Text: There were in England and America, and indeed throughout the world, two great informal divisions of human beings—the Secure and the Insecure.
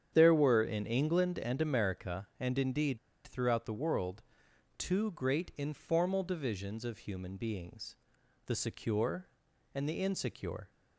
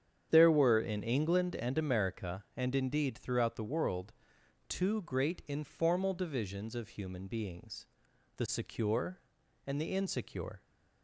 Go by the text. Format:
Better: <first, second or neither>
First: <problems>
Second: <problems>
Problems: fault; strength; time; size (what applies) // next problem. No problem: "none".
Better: second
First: starts louder than the rest; strong; until 1.1 s; 8.5 dB // pauses between "indeed" and "throughout"; slight; at 2.9 s; 0.27 s long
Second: starts louder than the rest; strong; until 1.3 s; 8 dB